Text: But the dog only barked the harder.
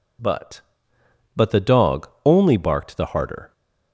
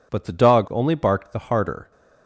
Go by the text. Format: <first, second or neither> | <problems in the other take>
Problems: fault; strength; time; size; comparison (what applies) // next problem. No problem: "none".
second | says "But" twice; at 1.3 s // pauses between "dog" and "only"; slight; at 2.0 s; 0.20 s long